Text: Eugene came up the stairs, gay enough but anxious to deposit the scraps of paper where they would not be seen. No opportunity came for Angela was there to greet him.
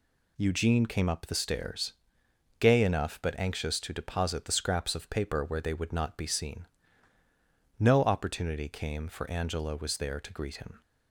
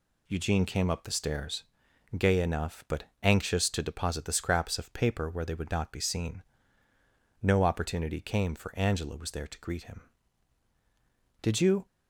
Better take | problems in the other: first | pauses between "but" and "anxious"; slight; at 3.0 s; 0.18 s long // goes on to say "Did you"; slight; from 11.4 s on; 0.44 s long

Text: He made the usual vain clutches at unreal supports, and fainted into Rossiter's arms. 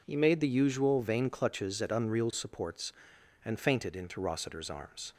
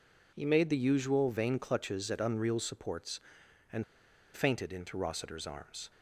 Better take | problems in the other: first | pauses between "and" and "fainted"; noticeable; at 3.8 s; 0.51 s long

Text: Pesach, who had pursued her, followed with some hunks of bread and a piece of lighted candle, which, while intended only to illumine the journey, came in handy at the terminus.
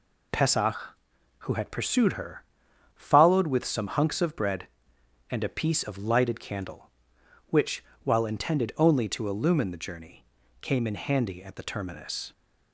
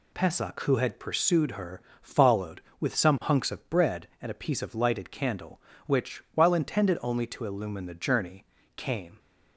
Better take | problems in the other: first | stops before "in handy at the terminus"; at 9.1 s

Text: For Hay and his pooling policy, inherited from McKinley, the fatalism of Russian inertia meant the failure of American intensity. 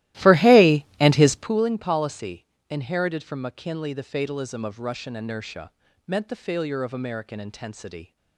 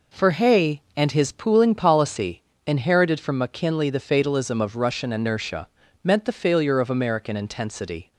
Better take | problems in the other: second | starts louder than the rest; strong; until 1.6 s; 16 dB // pauses between "inertia" and "meant"; slight; at 5.7 s; 0.36 s long; slight in the second

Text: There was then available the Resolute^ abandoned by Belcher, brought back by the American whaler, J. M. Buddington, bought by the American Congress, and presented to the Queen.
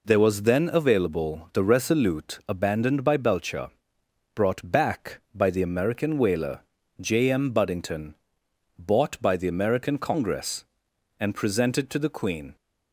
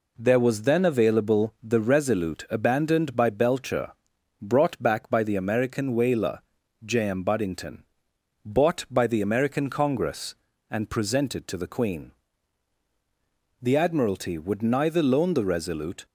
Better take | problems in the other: first | goes on to say "The admiralty would neither loan the Resolute"; strong; from 13.6 s on; 2.4 s long

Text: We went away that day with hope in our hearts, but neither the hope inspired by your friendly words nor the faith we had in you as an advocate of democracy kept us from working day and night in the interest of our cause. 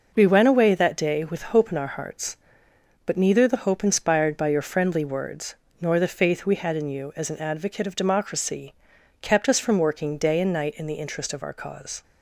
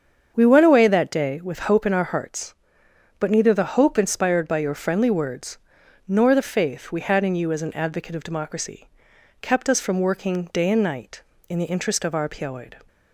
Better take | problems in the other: first | starts louder than the rest; strong; until 1.3 s; 7.5 dB // pauses between "words" and "nor"; noticeable; at 5.5 s; 0.48 s long; slight in the first // pauses between "democracy" and "kept"; noticeable; at 8.8 s; 0.52 s long; noticeable in the first // says "piaoid" for "cause"; at 12.2 s

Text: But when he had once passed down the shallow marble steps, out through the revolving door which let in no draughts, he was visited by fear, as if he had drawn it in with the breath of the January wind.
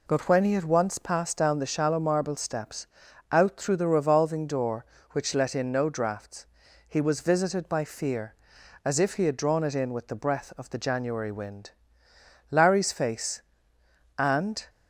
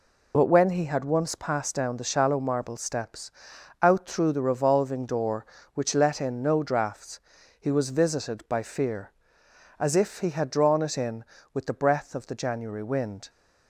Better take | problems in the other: second | goes on to say "Larry's face and"; strong; from 12.5 s on; 2.1 s long

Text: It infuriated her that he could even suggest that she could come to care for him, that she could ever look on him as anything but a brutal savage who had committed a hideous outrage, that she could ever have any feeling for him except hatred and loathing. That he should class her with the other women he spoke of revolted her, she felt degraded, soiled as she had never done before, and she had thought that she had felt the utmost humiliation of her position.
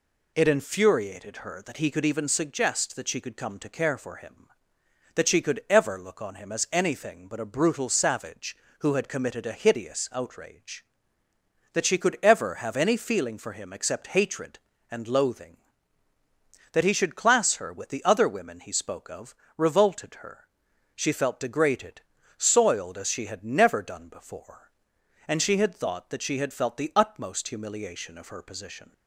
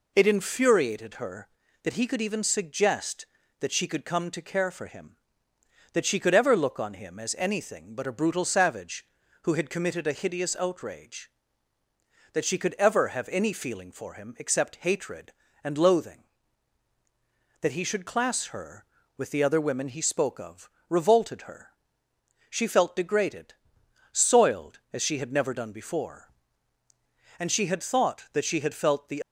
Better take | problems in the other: first | pauses between "of" and "revolted"; slight; at 20.6 s; 0.20 s long; slight in the first // stops before "utmost humiliation of her position"; at 29.2 s

